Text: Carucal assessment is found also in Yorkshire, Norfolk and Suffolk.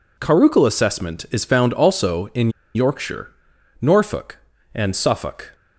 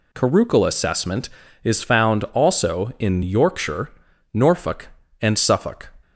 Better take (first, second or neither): second